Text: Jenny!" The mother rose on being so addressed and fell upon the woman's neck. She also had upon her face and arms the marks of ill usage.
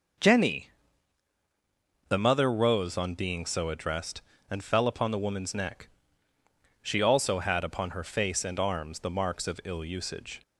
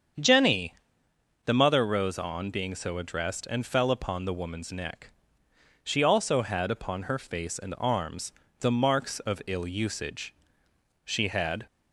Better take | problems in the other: first | starts louder than the rest; strong; until 1.9 s; 7.5 dB // pauses between "arms" and "the"; slight; at 8.3 s; 0.28 s long // goes on to say "She had"; noticeable; from 11.0 s on; 0.62 s long

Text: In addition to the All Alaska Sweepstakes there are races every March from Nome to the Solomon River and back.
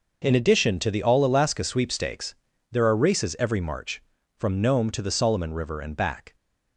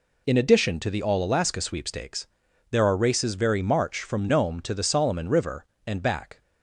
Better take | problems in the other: first | pauses between "Sweepstakes" and "there"; at 2.2 s; 0.44 s long; also in the first // says "very" for "every"; at 3.3 s

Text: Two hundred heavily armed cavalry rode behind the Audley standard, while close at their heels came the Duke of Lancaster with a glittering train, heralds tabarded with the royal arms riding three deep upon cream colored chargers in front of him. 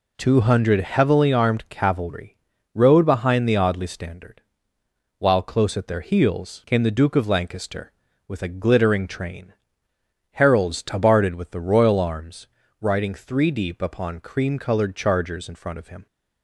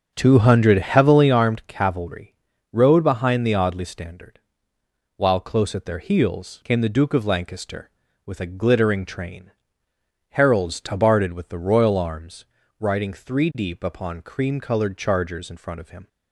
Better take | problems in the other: first | starts louder than the rest; until 1.5 s; 7 dB // pauses between "cavalry" and "rode"; slight; at 2.3 s; 0.36 s long; slight in the first // pauses between "arms" and "riding"; slight; at 12.4 s; 0.34 s long; slight in the first

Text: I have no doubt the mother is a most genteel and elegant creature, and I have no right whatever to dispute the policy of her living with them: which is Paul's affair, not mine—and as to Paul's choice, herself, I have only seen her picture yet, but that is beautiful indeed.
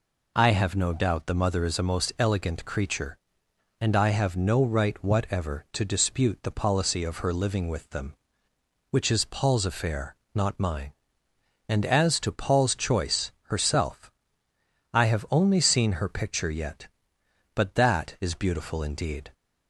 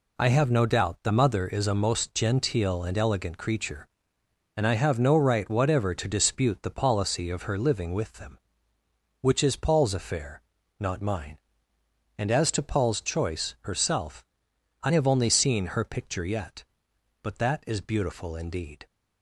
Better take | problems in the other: second | skips "genteel and"; at 2.1 s

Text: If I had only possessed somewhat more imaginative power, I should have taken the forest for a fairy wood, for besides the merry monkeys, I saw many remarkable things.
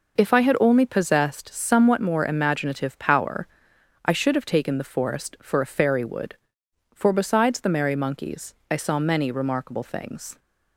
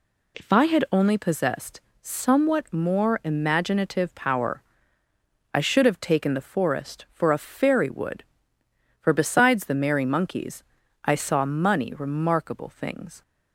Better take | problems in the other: first | pauses between "possessed" and "somewhat"; slight; at 1.7 s; 0.22 s long // says "money" for "many"; at 11.4 s

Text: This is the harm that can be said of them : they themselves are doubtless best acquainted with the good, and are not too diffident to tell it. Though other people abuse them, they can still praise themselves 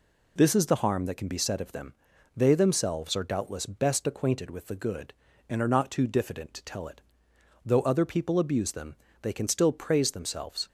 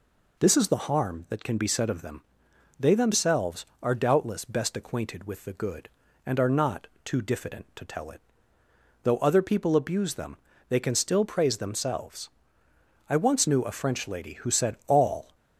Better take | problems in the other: first | pauses between "not" and "too"; slight; at 6.8 s; 0.18 s long // goes on to say "I once knew a French lady who said all"; strong; from 13.0 s on; 2.2 s long

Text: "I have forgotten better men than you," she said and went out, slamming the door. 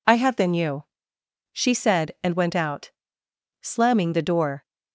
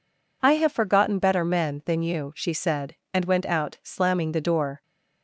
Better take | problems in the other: second | skips "forgotten better men"; at 0.3 s

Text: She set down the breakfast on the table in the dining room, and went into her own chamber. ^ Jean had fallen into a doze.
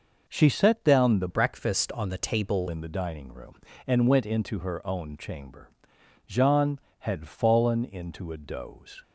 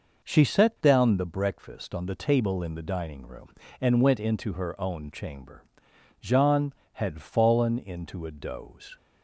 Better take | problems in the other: second | changes voice from "breakfast" to "table"; from 1.2 to 2.6 s; 1.4 s long

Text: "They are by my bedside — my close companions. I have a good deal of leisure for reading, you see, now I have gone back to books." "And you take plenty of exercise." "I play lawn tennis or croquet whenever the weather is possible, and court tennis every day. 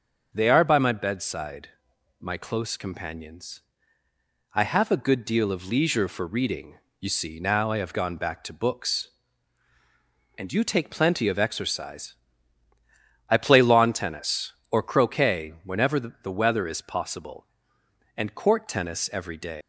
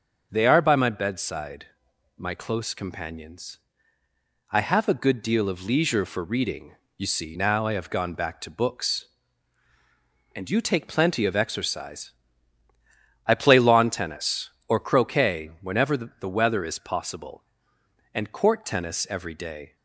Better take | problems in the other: second | leaves "day" unfinished; at 19.6 s; 170 ms

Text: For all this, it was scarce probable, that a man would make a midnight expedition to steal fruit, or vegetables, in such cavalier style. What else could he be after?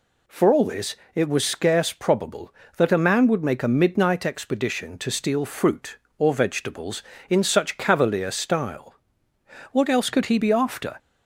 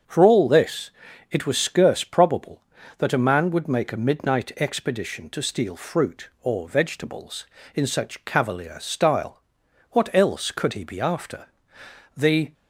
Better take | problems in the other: first | starts louder than the rest; until 1.4 s; 7 dB // goes on to say "The"; slight; from 12.1 s on; 0.36 s long

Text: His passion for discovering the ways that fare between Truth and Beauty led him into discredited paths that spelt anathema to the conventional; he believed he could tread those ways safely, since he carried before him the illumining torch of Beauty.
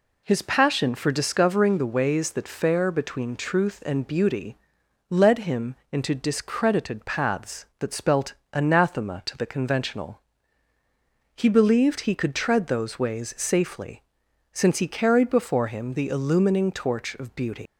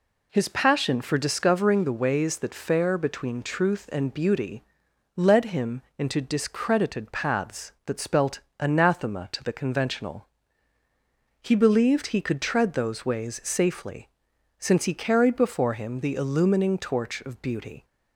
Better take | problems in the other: second | pauses between "Beauty" and "led"; noticeable; at 4.5 s; 0.54 s long; noticeable in the second // pauses between "him" and "into"; slight; at 5.7 s; 0.18 s long; slight in the second // pauses between "spelt" and "anathema"; slight; at 8.3 s; 0.22 s long; slight in the second // leaves "Beauty" unfinished; at 17.6 s; 125 ms

